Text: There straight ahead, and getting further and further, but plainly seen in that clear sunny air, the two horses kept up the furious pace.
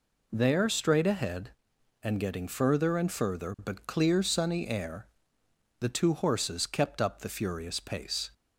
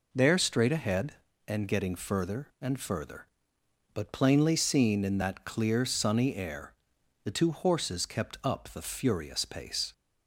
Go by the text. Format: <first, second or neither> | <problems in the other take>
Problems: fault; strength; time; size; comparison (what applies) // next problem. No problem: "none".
second | skips "plainly seen in that"; at 3.8 s